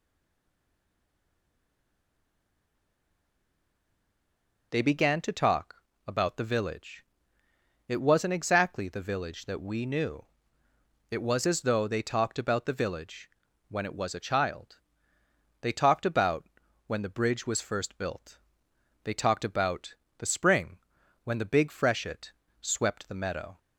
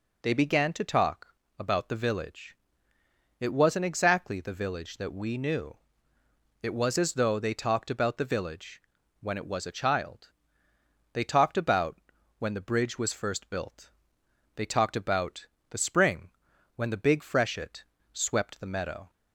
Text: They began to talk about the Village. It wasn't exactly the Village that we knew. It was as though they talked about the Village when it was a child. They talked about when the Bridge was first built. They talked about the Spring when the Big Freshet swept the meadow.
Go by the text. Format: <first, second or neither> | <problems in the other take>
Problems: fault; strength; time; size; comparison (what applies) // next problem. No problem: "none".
second | stays silent before the first word; strong; until 4.7 s; 4.7 s long // pauses between "talk" and "about"; slight; at 5.7 s; 0.32 s long; slight in the second // pauses between "Village" and "when"; at 13.2 s; 0.38 s long; also in the second // pauses between "about" and "when"; at 16.4 s; 0.40 s long; also in the second // pauses between "about" and "the"; slight; at 19.9 s; 0.24 s long; slight in the second // pauses between "Spring" and "when"; noticeable; at 20.7 s; 0.46 s long; noticeable in the second // pauses between "Freshet" and "swept"; slight; at 22.3 s; 0.28 s long; slight in the second